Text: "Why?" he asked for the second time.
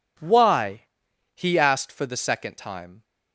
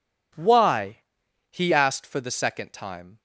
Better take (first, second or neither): neither